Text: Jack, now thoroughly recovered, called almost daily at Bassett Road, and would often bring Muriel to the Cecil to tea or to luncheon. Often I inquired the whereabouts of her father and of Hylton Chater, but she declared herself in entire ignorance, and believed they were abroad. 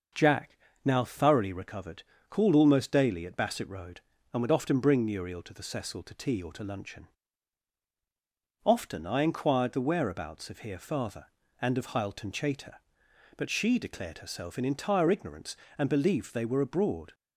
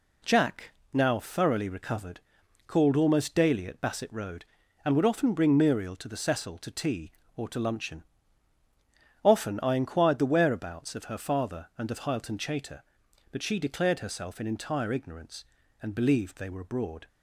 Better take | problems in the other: second | starts louder than the rest; noticeable; until 1.4 s; 6 dB // says "here" for "her"; at 10.5 s

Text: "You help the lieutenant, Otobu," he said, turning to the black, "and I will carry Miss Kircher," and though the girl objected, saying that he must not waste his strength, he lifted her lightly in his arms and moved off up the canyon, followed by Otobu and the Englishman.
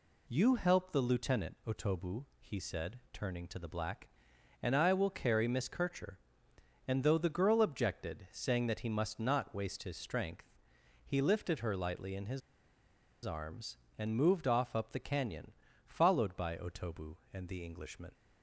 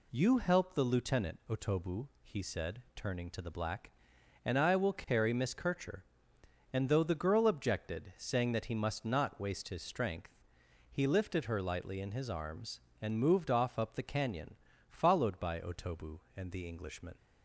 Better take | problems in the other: second | pauses between "his" and "arms"; noticeable; at 12.4 s; 0.84 s long

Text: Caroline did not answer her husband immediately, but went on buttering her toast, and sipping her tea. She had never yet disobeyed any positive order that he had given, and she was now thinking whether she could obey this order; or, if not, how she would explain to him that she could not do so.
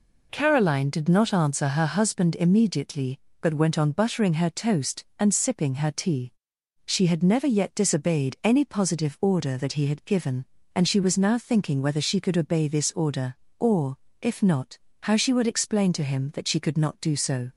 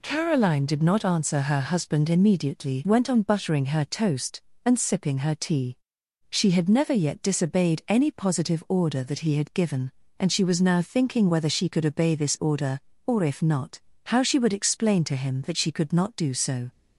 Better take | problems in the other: first | skips "but"; at 2.8 s

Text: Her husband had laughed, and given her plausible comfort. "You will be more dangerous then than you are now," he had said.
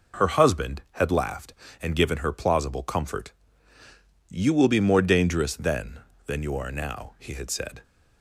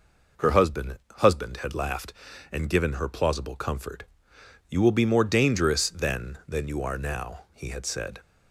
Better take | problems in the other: first | says "husband" twice; at 1.1 s

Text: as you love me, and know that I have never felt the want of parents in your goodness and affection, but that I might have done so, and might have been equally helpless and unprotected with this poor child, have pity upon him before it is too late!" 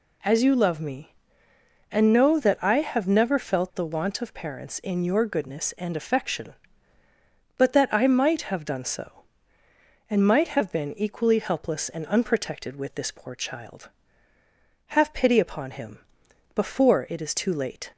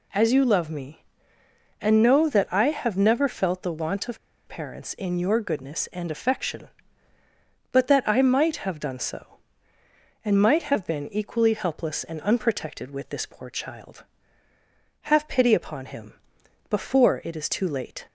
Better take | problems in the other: first | pauses between "of" and "parents"; slight; at 4.1 s; 0.29 s long // pauses between "him" and "before"; noticeable; at 16.1 s; 0.56 s long; noticeable in the first

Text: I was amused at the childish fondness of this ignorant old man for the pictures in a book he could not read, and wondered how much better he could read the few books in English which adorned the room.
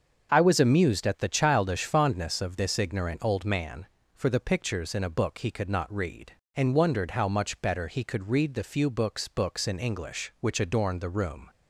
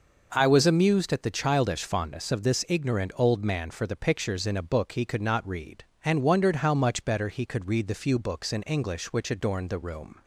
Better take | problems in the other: second | starts louder than the rest; until 1.3 s; 6.5 dB // says "books" twice; at 9.2 s

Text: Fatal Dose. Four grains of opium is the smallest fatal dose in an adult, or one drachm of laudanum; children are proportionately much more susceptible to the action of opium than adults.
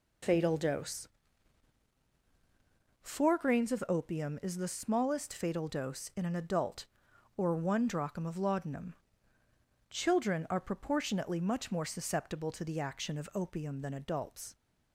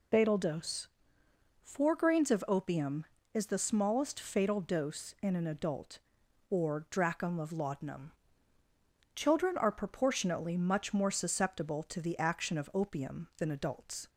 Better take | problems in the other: first | skips "one"; at 6.8 s

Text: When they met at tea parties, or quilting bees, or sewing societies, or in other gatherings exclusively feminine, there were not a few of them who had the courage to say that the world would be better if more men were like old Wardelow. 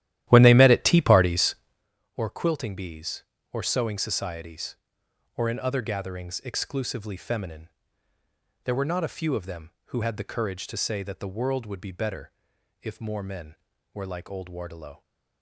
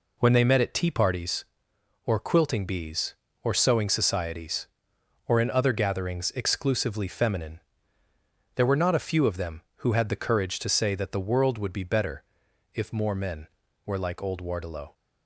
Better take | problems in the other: second | starts louder than the rest; strong; until 1.9 s; 13 dB // pauses between "better" and "if"; noticeable; at 12.3 s; 0.50 s long; noticeable in the second

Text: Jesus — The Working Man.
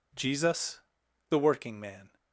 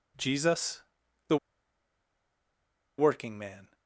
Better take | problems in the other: first | pauses between "The" and "Working"; strong; at 1.3 s; 1.6 s long

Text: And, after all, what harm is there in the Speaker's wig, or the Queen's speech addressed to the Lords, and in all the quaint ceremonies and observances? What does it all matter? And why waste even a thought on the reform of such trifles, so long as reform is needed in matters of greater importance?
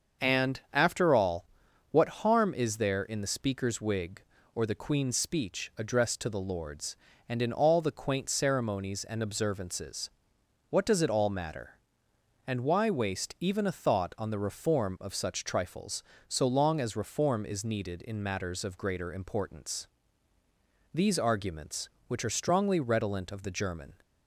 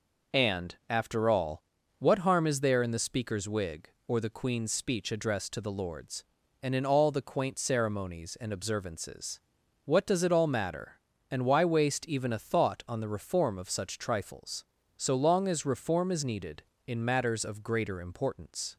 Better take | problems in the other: second | starts louder than the rest; until 1.3 s; 6.5 dB // goes on to say "These arguments which are strongly redolent of the German"; strong; from 20.9 s on; 3.0 s long

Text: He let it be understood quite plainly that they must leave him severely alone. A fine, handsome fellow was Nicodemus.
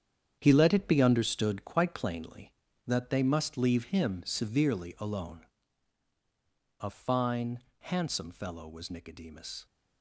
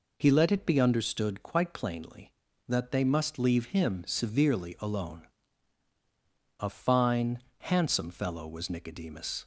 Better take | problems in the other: second | gets quieter; strong; throughout; 10.5 dB

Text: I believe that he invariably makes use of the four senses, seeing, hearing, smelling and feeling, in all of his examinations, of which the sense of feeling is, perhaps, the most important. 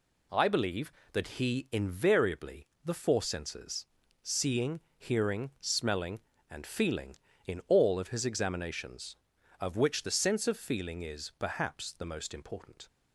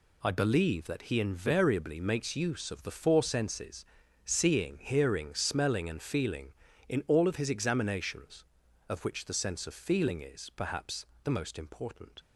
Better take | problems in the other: second | skips "makes use of"; at 2.7 s

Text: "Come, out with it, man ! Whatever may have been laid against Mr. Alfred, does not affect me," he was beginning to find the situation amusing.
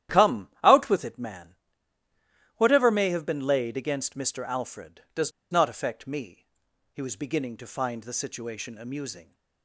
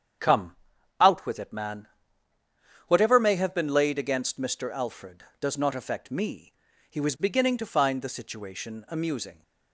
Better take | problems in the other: second | starts louder than the rest; strong; until 1.2 s; 11.5 dB; strong in the second // pauses between "does" and "not"; slight; at 5.3 s; 0.20 s long

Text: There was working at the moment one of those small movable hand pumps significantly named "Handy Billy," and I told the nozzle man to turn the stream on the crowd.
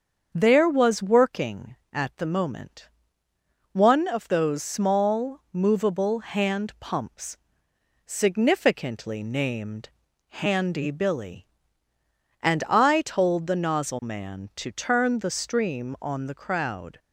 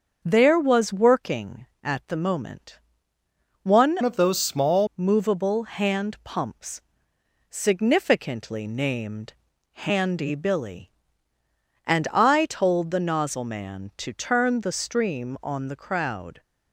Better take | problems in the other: first | starts louder than the rest; until 1.2 s; 6.5 dB; also in the first // pauses between "moment" and "one"; noticeable; at 2.7 s; 0.86 s long; noticeable in the first // changes voice from "of" to "small"; from 4.0 to 4.8 s; 0.8 s long // pauses between "pumps" and "significantly"; noticeable; at 6.8 s; 0.70 s long; noticeable in the first // pauses between "named" and "Handy"; at 9.3 s; 0.40 s long; also in the first

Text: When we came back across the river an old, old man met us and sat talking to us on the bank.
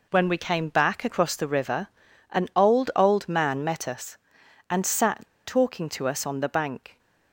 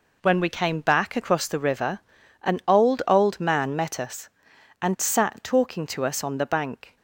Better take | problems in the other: second | pauses between "river" and "an"; at 1.8 s; 0.42 s long; also in the second // pauses between "sat" and "talking"; slight; at 5.2 s; 0.19 s long

